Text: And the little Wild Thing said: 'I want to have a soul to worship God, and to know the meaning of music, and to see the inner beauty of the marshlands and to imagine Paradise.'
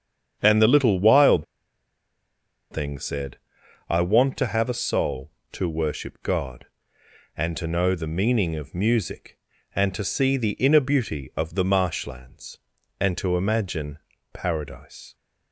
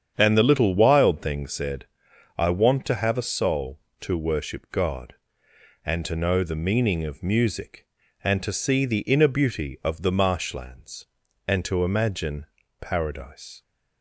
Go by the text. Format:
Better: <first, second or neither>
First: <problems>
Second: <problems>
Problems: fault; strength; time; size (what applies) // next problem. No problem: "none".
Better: second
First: starts louder than the rest; strong; until 1.4 s; 8 dB // pauses between "Wild" and "Thing"; strong; at 1.4 s; 1.2 s long // pauses between "imagine" and "Paradise"; slight; at 13.9 s; 0.34 s long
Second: starts louder than the rest; strong; until 1.1 s; 8 dB // pauses between "imagine" and "Paradise"; slight; at 12.4 s; 0.34 s long